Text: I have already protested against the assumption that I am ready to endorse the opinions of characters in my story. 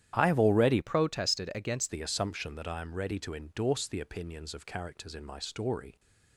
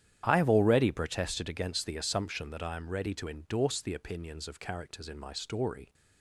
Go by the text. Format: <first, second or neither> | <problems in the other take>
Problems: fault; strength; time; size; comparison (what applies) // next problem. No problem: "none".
second | starts louder than the rest; strong; until 1.1 s; 11 dB; strong in the second // changes voice from "protested" to "against"; from 0.8 to 1.9 s; 1.1 s long